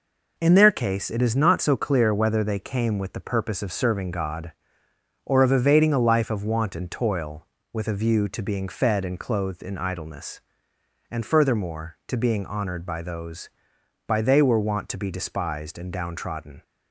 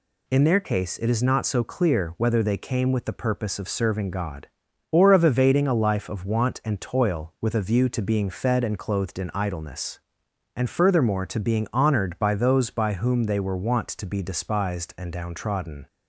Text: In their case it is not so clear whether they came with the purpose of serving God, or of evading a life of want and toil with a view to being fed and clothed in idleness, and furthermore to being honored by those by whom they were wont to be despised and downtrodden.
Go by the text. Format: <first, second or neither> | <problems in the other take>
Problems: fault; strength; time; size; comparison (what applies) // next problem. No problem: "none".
second | skips "whom"; at 14.2 s